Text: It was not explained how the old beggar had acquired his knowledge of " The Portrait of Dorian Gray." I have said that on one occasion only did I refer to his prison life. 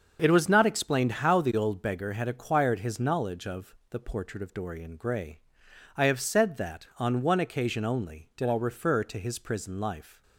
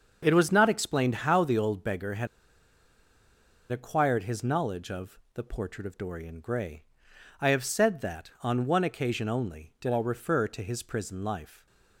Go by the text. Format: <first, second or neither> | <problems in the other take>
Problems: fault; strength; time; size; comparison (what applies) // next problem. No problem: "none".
first | starts louder than the rest; until 1.2 s; 6.5 dB; also in the first // pauses between "had" and "acquired"; strong; at 2.2 s; 1.4 s long